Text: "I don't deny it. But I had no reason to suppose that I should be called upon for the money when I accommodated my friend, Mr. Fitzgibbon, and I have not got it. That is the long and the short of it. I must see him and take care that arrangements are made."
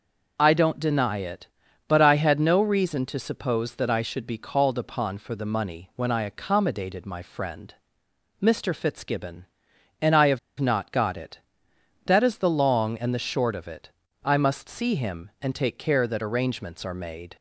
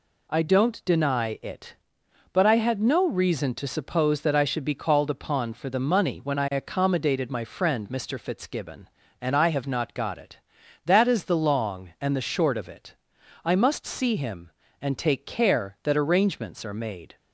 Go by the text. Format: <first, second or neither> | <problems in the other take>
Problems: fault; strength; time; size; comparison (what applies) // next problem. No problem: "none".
second | pauses between "have" and "not"; slight; at 10.3 s; 0.20 s long